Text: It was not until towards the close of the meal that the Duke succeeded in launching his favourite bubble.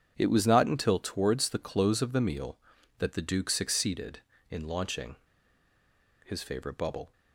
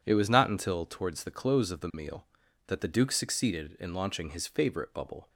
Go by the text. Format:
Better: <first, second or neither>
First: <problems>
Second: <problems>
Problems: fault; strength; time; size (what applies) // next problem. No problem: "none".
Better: second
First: starts louder than the rest; strong; until 1.1 s; 8 dB // pauses between "launching" and "his"; at 5.1 s; 1.0 s long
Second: none